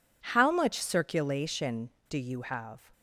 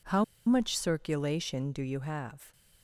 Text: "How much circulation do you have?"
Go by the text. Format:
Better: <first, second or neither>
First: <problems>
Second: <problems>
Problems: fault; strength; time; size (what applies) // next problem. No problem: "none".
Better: first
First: none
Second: pauses between "How" and "much"; slight; at 0.2 s; 0.23 s long